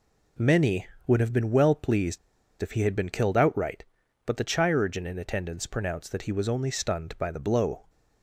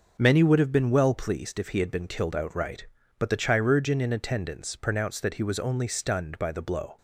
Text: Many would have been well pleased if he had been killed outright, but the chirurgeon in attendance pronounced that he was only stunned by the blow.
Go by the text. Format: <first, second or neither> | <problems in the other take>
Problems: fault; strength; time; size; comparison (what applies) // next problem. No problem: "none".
second | pauses between "pleased" and "if"; at 2.1 s; 0.43 s long